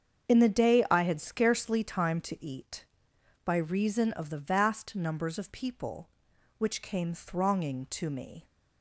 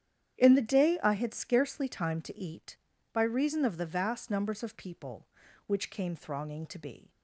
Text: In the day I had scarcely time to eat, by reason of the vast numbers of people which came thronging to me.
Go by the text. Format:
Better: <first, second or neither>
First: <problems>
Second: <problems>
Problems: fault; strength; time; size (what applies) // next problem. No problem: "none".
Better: first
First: starts louder than the rest; strong; until 1.3 s; 7.5 dB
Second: starts louder than the rest; strong; until 1.4 s; 10 dB // says "be" for "me"; at 6.7 s